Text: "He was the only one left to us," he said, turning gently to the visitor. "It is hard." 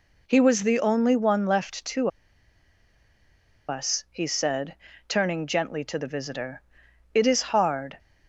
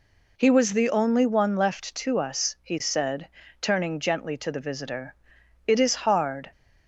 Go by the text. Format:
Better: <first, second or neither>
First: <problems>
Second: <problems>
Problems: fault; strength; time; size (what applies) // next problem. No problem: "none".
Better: second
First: pauses between "to" and "us"; strong; at 2.0 s; 1.6 s long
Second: none